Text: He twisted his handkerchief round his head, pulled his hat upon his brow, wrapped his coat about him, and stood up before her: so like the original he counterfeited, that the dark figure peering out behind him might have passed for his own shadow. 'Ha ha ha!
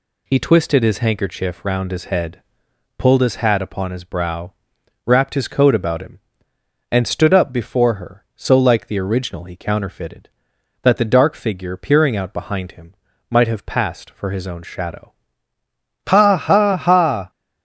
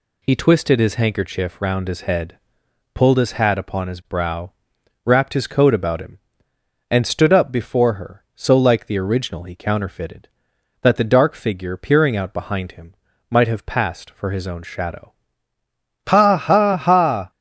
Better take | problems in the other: neither | pauses between "him" and "might"; slight; the same in both

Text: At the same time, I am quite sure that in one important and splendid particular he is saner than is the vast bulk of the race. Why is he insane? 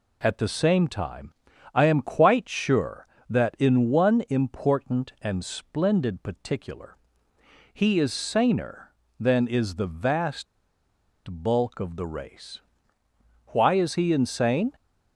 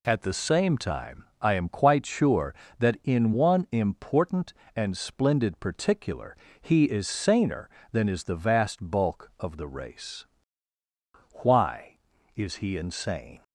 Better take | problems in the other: second | pauses between "particular" and "he"; noticeable; at 6.9 s; 0.78 s long; slight in the second // pauses between "vast" and "bulk"; noticeable; at 10.4 s; 0.83 s long

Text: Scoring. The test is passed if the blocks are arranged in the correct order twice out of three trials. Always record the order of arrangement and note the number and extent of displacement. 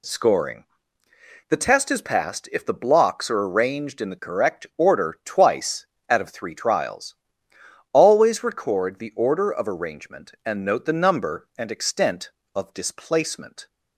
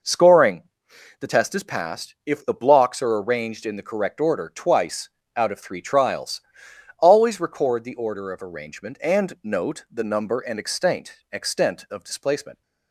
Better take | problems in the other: first | pauses between "twice" and "out"; slight; at 5.0 s; 0.28 s long; slight in the first // says "extent" twice; at 11.3 s

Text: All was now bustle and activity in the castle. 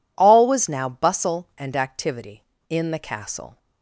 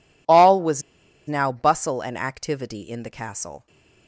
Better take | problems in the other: first | pauses between "was" and "now"; noticeable; at 0.8 s; 0.46 s long

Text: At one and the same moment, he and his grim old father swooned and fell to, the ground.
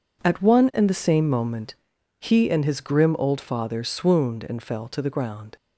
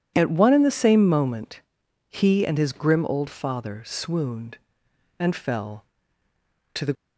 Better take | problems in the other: first | stops before "ground"; at 6.9 s

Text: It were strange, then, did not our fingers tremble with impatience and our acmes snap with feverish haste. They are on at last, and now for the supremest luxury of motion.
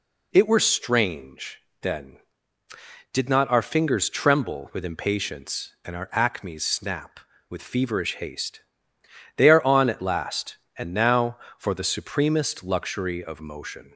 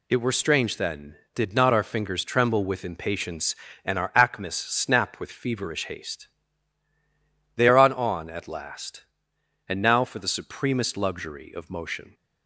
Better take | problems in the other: first | says "on" twice; at 7.9 s

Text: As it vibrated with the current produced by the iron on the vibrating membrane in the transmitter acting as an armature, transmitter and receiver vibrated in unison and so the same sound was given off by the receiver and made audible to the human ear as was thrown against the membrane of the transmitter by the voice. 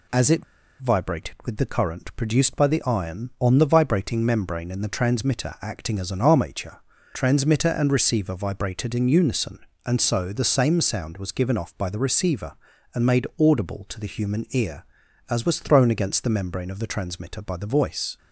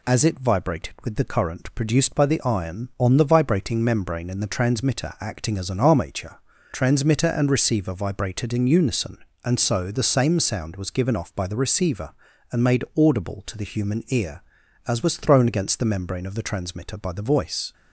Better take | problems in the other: second | pauses between "it" and "vibrated"; at 0.4 s; 0.37 s long

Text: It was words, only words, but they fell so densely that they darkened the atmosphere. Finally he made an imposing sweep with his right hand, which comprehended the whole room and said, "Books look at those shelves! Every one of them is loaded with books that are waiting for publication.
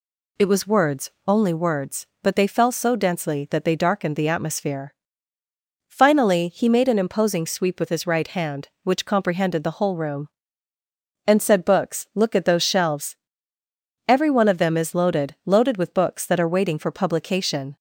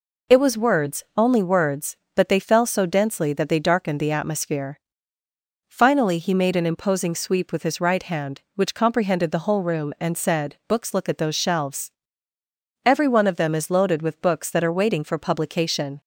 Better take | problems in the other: second | says "loaded" twice; at 15.4 s

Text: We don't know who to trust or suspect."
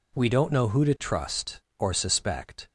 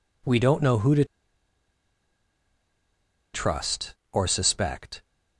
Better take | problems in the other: first | pauses between "to" and "trust"; strong; at 1.0 s; 2.2 s long

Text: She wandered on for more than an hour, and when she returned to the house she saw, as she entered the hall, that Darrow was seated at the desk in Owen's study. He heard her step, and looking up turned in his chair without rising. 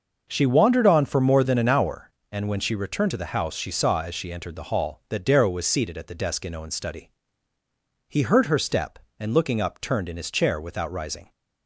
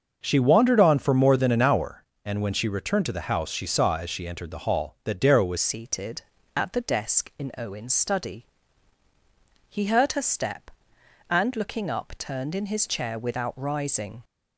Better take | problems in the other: first | starts louder than the rest; until 1.2 s; 6.5 dB // changes voice at "seated"; from 5.5 s on; 8.7 s long

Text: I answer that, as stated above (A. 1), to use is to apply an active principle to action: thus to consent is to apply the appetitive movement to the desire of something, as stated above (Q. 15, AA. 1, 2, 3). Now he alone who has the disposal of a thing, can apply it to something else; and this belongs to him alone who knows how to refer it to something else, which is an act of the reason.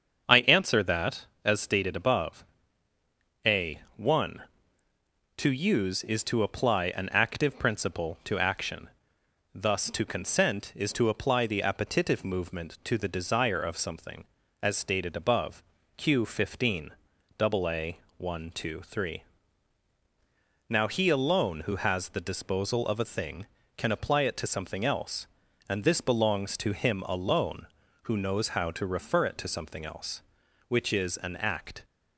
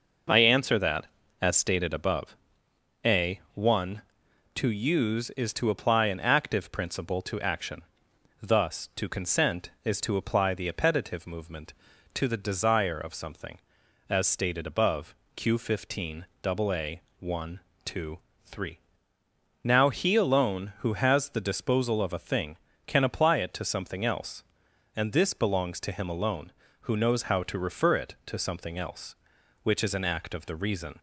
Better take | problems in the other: second | starts louder than the rest; until 1.4 s; 7 dB // stops before "of the reason"; at 31.8 s

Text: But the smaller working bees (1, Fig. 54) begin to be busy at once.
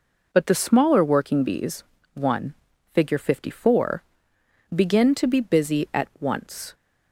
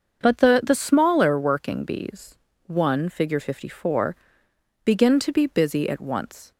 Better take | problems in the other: first | starts louder than the rest; until 1.2 s; 6.5 dB // says "the" twice; at 0.6 s

